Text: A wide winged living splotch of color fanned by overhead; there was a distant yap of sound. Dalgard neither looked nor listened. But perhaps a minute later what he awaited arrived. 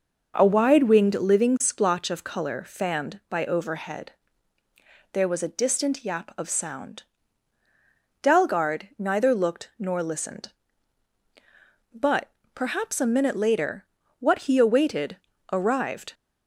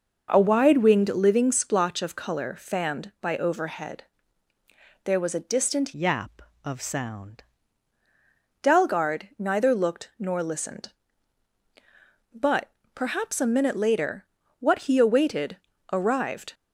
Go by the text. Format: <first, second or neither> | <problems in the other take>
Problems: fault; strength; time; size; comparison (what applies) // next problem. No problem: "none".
first | changes voice from "yap" to "sound"; from 5.9 to 7.4 s; 1.5 s long // pauses between "But" and "perhaps"; slight; at 12.6 s; 0.24 s long; slight in the first // pauses between "later" and "what"; slight; at 14.2 s; 0.34 s long; slight in the first // pauses between "awaited" and "arrived"; slight; at 15.5 s; 0.36 s long; slight in the first